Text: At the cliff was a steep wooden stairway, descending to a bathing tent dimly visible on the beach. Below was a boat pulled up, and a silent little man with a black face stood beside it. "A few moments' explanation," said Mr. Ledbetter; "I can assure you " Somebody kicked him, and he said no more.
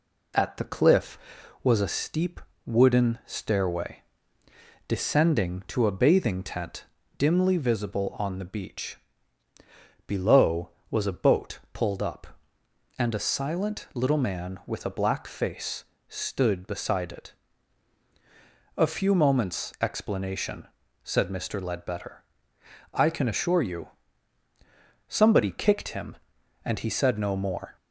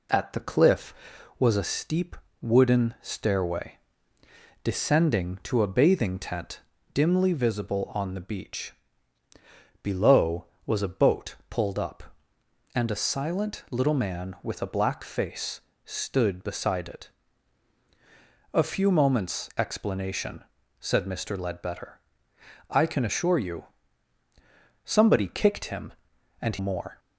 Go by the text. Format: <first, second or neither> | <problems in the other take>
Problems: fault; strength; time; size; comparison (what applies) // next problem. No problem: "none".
first | pauses between "steep" and "wooden"; slight; at 2.1 s; 0.24 s long; slight in the first // pauses between "tent" and "dimly"; slight; at 6.6 s; 0.32 s long; slight in the first // pauses between "face" and "stood"; slight; at 15.6 s; 0.24 s long; slight in the first // skips "he said no"; at 26.5 s